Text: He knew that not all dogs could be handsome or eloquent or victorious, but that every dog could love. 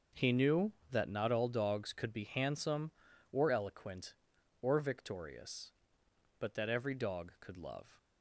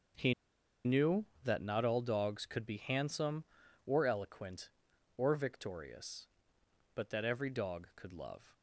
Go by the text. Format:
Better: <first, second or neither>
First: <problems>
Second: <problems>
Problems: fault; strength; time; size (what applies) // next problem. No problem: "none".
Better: first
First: starts louder than the rest; noticeable; until 1.3 s; 6 dB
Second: starts louder than the rest; noticeable; until 1.8 s; 6 dB // pauses between "He" and "knew"; noticeable; at 0.3 s; 0.51 s long